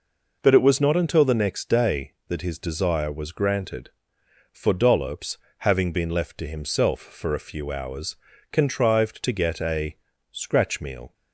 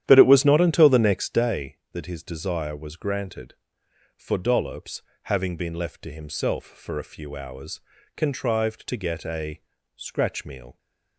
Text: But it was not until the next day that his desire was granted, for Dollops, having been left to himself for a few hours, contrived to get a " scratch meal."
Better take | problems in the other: first | starts louder than the rest; strong; until 1.5 s; 11 dB

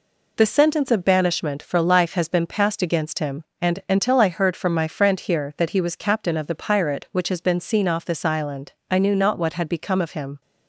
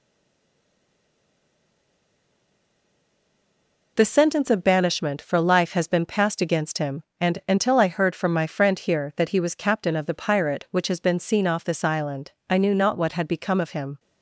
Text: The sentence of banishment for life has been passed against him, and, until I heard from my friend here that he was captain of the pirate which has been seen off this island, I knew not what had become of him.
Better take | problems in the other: first | stays silent before the first word; strong; until 3.9 s; 3.9 s long

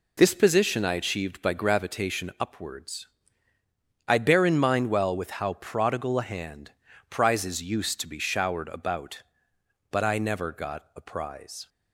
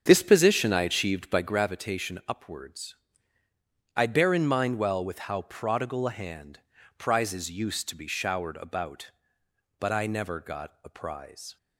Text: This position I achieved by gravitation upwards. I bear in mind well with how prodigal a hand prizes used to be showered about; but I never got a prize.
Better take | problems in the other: first | starts louder than the rest; strong; until 1.5 s; 7 dB // pauses between "hand" and "prizes"; slight; at 6.6 s; 0.36 s long; slight in the first

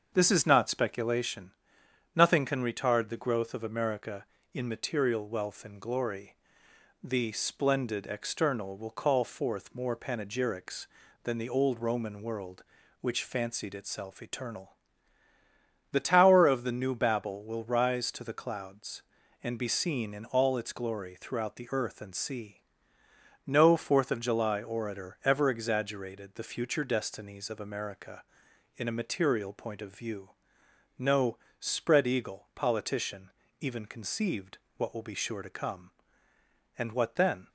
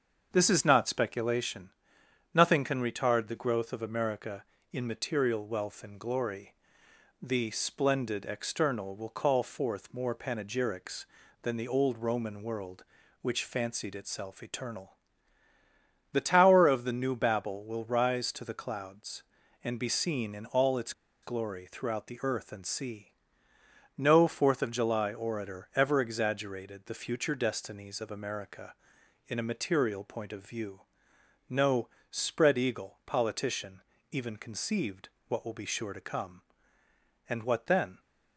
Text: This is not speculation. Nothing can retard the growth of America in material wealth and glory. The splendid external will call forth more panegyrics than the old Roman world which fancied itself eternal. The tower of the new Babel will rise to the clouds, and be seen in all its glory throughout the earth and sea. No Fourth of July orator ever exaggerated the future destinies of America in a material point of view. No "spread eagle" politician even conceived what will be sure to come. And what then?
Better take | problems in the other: first | starts louder than the rest; until 1.3 s; 6.5 dB; also in the first // pauses between "its" and "glory"; slight; at 20.9 s; 0.31 s long // pauses between "No" and "spread"; slight; at 31.8 s; 0.22 s long; slight in the first // pauses between "politician" and "even"; slight; at 33.8 s; 0.30 s long; slight in the first // pauses between "conceived" and "what"; slight; at 35.0 s; 0.18 s long; slight in the first

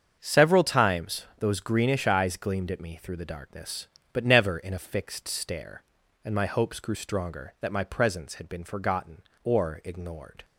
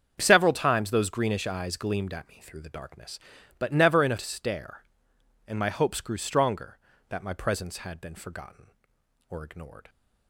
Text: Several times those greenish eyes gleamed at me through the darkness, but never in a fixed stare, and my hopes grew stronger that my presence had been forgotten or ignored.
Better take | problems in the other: first | starts louder than the rest; strong; until 1.2 s; 7 dB; also in the first // skips "fixed"; at 4.1 s

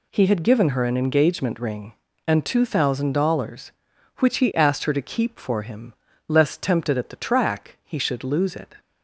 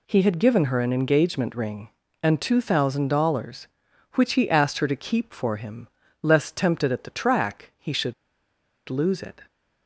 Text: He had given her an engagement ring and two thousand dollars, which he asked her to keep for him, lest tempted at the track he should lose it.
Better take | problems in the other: first | pauses between "should" and "lose"; noticeable; at 8.1 s; 0.75 s long

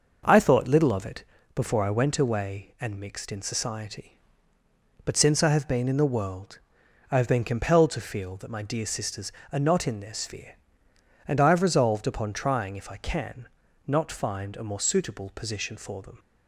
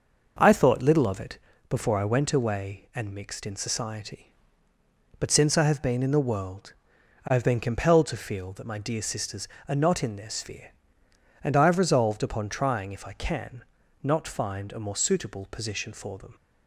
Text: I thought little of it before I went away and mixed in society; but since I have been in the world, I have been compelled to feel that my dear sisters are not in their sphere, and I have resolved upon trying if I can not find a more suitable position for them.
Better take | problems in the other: neither | starts louder than the rest; the same in both // pauses between "it" and "before"; slight; the same in both // pauses between "can" and "not"; slight; the same in both

